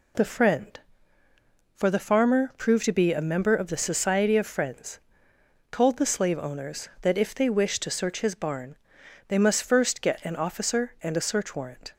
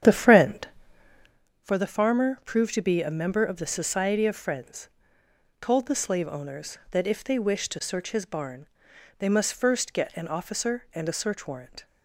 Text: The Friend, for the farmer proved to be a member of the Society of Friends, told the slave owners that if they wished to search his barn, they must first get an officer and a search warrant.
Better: first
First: none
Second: starts louder than the rest; strong; until 1.4 s; 9 dB

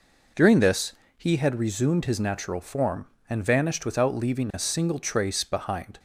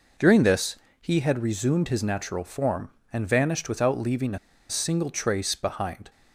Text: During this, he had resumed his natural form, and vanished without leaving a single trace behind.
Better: first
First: none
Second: pauses between "a" and "single"; slight; at 4.3 s; 0.31 s long

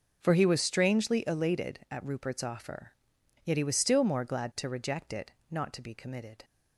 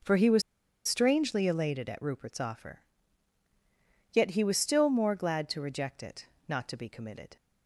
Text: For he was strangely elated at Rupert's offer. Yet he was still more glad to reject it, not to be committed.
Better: first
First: starts louder than the rest; until 1.2 s; 6 dB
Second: starts louder than the rest; noticeable; until 1.4 s; 6 dB // pauses between "was" and "strangely"; noticeable; at 0.4 s; 0.46 s long

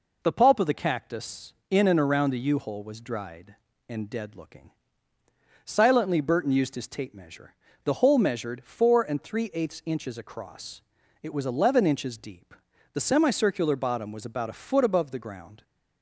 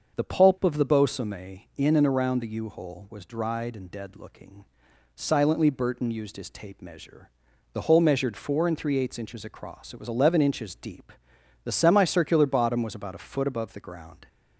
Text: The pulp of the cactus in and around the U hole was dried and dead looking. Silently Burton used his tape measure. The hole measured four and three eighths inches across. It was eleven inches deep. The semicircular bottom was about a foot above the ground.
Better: first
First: none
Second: starts louder than the rest; until 1.2 s; 6.5 dB // says "bosome" for "cactus"; at 0.8 s

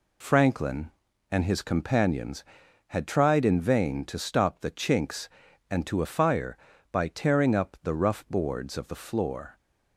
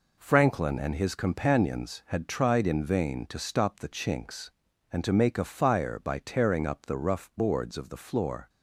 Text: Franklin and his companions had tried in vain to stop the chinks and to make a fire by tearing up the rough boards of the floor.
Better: second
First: skips "make"; at 6.0 s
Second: none

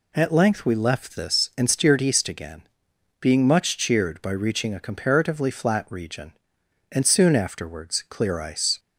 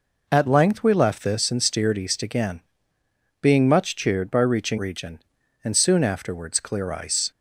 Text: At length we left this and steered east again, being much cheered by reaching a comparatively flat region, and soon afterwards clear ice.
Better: first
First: none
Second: skips "a comparatively flat"; at 4.7 s

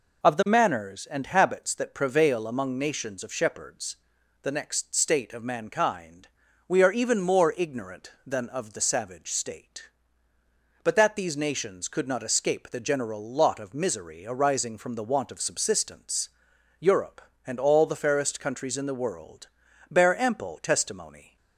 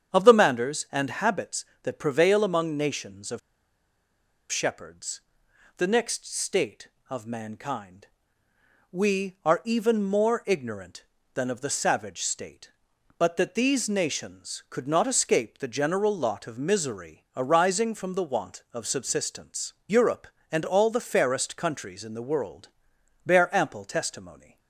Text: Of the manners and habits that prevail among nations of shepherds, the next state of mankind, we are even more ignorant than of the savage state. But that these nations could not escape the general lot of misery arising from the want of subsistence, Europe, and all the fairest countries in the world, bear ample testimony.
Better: first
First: none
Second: starts louder than the rest; strong; until 1.1 s; 8 dB // pauses between "of" and "shepherds"; at 3.3 s; 1.1 s long

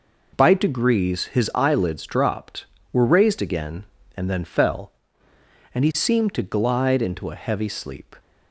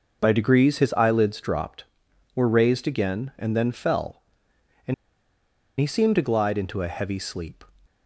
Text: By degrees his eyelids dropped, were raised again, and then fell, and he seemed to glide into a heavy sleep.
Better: first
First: none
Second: pauses between "and" and "he"; noticeable; at 4.9 s; 0.85 s long

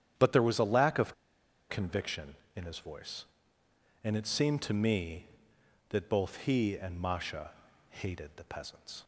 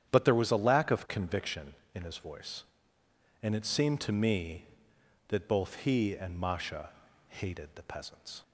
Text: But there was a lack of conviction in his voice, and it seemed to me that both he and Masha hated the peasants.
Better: second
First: starts louder than the rest; strong; until 1.7 s; 9.5 dB // pauses between "of" and "conviction"; noticeable; at 1.1 s; 0.56 s long // pauses between "Masha" and "hated"; at 7.5 s; 0.38 s long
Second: starts louder than the rest; strong; until 1.1 s; 9.5 dB // pauses between "Masha" and "hated"; at 6.9 s; 0.38 s long

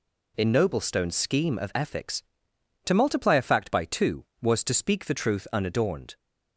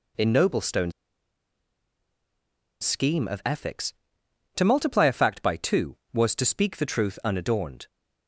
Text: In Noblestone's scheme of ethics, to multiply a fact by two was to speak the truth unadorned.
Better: first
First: none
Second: pauses between "Noblestone's" and "scheme"; strong; at 0.9 s; 1.9 s long

